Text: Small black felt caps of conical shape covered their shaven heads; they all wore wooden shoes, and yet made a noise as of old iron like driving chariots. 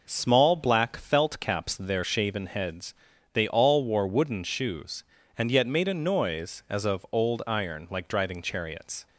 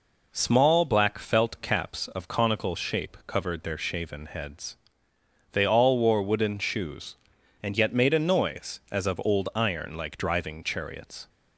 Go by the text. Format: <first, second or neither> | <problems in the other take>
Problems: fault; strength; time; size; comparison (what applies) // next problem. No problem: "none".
second | skips "of conical shape covered"; at 1.7 s